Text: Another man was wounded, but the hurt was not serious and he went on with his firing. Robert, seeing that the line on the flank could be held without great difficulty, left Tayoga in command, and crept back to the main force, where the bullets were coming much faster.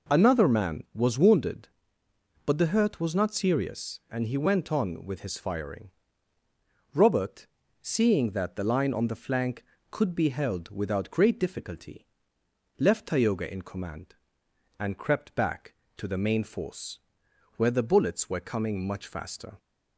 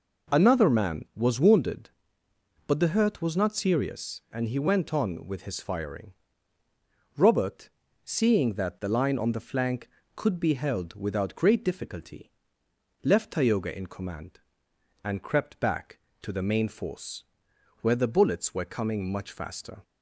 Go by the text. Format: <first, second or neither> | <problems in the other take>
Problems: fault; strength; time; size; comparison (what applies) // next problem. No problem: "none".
neither | none